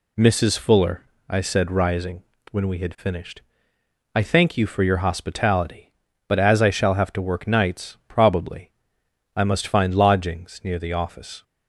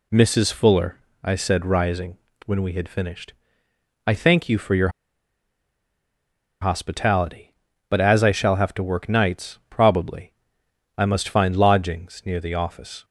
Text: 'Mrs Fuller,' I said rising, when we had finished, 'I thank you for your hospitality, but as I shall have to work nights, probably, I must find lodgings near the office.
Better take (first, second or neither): first